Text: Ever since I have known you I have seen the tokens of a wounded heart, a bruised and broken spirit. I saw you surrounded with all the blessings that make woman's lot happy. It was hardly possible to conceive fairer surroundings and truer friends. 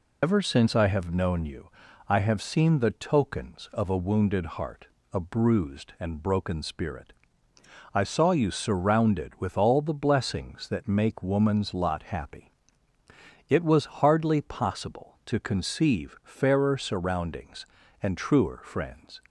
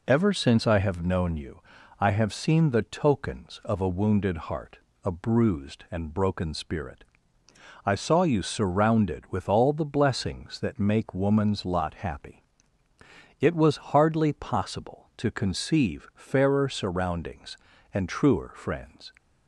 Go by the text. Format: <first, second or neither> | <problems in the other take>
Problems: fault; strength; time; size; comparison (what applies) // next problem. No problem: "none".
second | loses the start of "Ever"; at 0.2 s; 60 ms // pauses between "you" and "I"; at 1.6 s; 0.40 s long; also in the second